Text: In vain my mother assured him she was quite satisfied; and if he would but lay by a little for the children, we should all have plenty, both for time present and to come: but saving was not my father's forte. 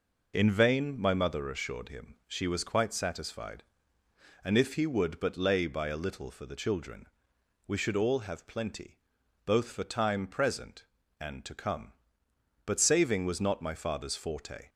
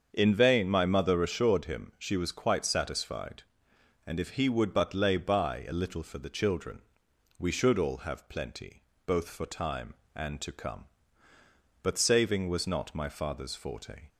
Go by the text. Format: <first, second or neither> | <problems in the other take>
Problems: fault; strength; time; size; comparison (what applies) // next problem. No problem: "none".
first | starts louder than the rest; until 1.1 s; 7 dB // skips "present"; at 10.0 s